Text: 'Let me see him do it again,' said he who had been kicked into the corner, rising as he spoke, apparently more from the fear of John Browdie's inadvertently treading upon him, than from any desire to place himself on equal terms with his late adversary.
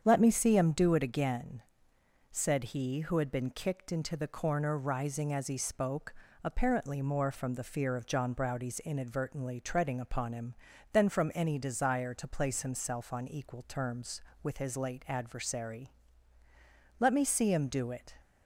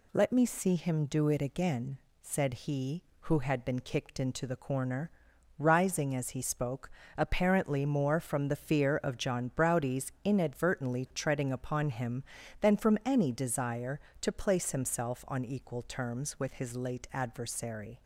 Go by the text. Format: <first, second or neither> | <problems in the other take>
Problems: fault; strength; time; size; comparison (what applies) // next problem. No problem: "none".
second | starts louder than the rest; strong; until 1.0 s; 8 dB // goes on to say "Let me see him do it"; noticeable; from 16.9 s on; 1.1 s long